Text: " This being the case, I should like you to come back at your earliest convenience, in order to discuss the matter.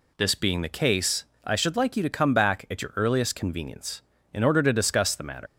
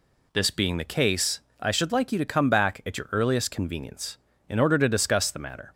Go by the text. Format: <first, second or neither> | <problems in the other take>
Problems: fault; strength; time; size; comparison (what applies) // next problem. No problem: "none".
second | leaves "matter" unfinished; at 5.4 s; 95 ms